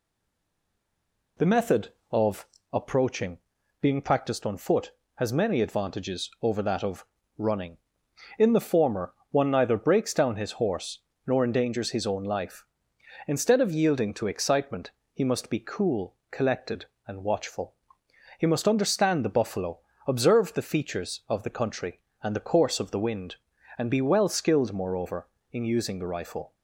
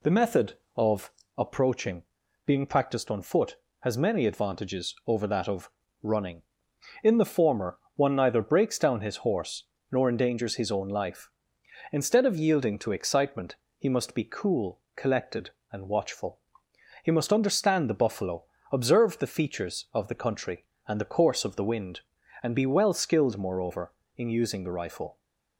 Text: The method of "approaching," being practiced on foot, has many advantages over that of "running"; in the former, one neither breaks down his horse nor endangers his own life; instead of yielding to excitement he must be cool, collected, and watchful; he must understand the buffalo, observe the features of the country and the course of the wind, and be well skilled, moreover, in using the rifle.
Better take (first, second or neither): second